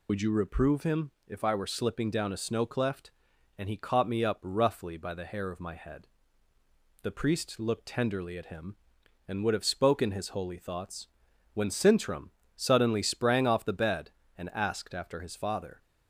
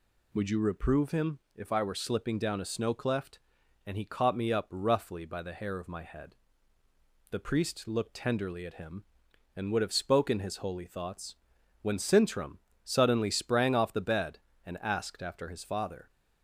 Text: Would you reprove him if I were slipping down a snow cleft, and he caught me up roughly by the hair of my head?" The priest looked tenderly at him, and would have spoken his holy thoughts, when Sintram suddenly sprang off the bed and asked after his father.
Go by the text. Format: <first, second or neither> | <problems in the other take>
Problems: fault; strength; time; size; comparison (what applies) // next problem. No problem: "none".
second | loses the start of "Would"; at 0.0 s; 35 ms // pauses between "him" and "if"; slight; at 1.1 s; 0.16 s long; slight in the second // pauses between "Sintram" and "suddenly"; slight; at 12.2 s; 0.26 s long; slight in the second